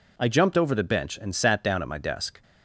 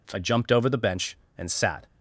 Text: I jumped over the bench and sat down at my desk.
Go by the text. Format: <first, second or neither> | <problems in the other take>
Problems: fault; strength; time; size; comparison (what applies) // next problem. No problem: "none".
first | stops before "down at my desk"; at 1.8 s